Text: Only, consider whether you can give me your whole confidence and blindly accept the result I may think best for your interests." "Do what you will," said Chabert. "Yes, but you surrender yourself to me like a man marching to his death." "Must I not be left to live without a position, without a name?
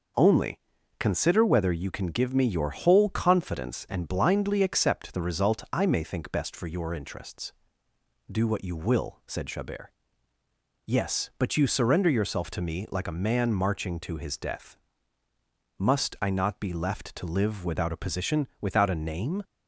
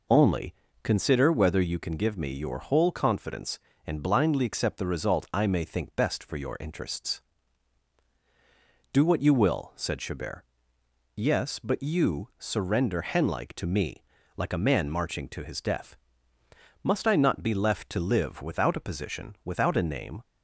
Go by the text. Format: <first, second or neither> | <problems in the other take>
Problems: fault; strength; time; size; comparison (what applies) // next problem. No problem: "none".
first | says "henlike" for "yourself"; at 13.0 s // pauses between "me" and "like"; slight; at 14.0 s; 0.36 s long